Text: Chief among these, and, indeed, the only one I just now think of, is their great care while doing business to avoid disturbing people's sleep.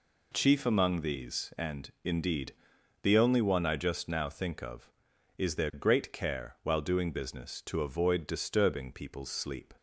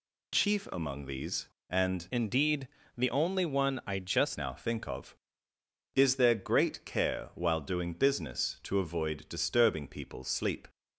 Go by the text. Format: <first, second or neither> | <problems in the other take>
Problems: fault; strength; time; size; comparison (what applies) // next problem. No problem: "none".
first | changes voice from "indeed" to "just"; from 2.1 to 4.3 s; 2.2 s long